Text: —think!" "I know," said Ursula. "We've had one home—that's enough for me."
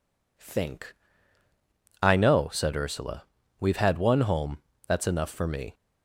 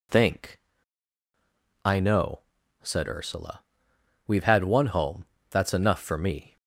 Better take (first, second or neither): neither